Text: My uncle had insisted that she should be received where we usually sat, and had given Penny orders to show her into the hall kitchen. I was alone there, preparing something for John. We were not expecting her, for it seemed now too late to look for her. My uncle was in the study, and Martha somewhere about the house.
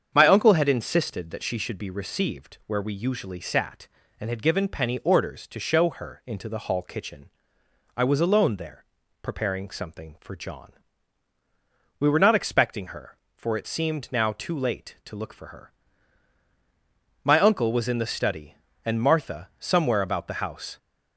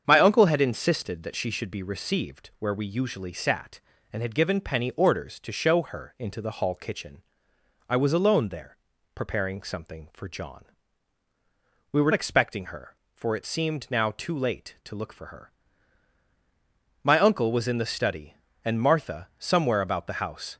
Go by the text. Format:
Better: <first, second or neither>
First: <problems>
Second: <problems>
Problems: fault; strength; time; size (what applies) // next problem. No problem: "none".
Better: first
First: starts louder than the rest; strong; until 1.1 s; 7.5 dB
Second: starts louder than the rest; strong; until 1.0 s; 7.5 dB // skips "not"; at 12.1 s